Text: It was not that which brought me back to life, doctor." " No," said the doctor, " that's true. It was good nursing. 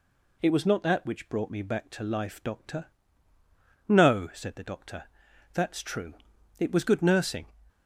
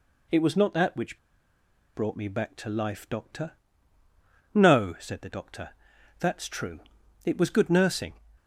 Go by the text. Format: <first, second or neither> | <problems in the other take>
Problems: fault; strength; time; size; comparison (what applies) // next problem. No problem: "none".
first | pauses between "which" and "brought"; noticeable; at 1.1 s; 0.76 s long